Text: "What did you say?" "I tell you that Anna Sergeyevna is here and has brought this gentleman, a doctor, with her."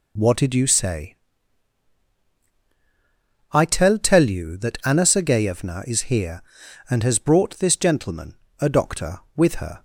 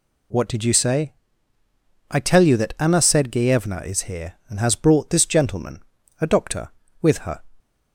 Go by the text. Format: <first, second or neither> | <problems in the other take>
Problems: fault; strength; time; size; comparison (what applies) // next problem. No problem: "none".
second | says "tell" twice; at 3.9 s